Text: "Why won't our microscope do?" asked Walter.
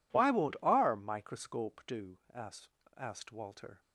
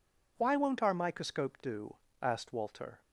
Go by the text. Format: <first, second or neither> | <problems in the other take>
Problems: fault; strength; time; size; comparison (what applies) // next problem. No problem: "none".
second | says "asked" twice; at 2.9 s